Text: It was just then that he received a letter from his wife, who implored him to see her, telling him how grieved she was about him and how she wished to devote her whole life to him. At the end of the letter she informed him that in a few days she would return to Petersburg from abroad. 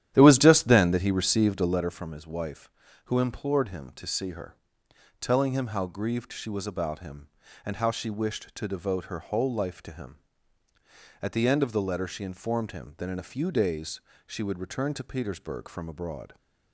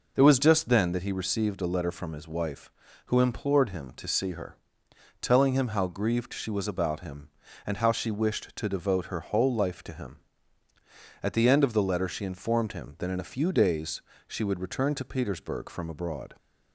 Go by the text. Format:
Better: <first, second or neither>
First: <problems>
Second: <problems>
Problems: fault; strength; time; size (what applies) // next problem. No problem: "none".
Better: second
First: starts louder than the rest; strong; until 2.0 s; 11.5 dB // pauses between "days" and "she"; slight; at 14.0 s; 0.24 s long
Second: pauses between "days" and "she"; slight; at 14.0 s; 0.24 s long